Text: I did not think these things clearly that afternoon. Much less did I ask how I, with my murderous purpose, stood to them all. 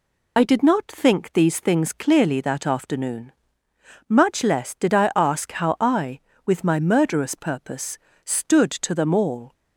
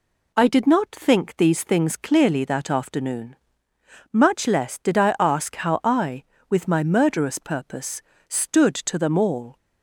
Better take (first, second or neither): second